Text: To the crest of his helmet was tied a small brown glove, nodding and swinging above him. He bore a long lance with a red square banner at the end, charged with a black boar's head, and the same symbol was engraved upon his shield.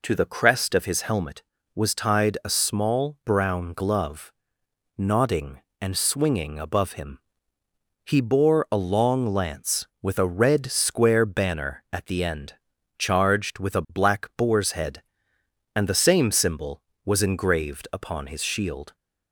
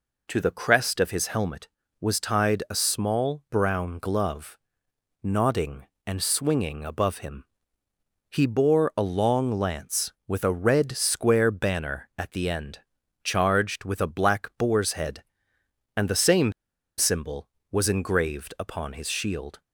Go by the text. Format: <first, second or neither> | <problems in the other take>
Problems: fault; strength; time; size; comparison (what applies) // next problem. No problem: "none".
first | pauses between "same" and "symbol"; noticeable; at 16.5 s; 0.46 s long